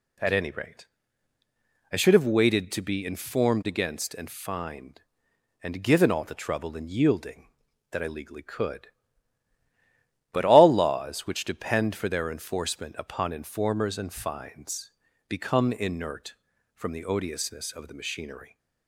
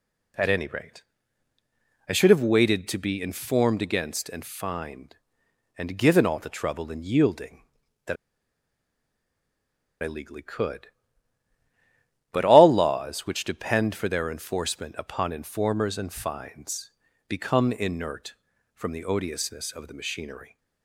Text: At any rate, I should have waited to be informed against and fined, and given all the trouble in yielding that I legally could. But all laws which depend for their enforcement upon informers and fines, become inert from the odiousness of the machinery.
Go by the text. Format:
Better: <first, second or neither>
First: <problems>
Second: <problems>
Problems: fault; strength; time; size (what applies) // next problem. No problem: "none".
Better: first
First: none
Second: pauses between "that" and "I"; strong; at 8.1 s; 1.8 s long